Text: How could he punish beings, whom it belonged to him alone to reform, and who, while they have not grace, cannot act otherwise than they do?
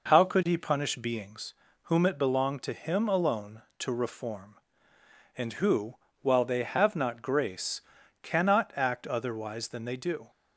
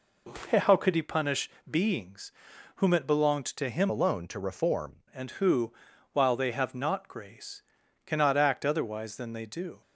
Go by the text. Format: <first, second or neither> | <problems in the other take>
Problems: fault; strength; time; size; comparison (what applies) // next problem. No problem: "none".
first | pauses between "punish" and "beings"; slight; at 1.4 s; 0.20 s long // changes voice from "alone" to "reform"; from 3.8 to 5.0 s; 1.2 s long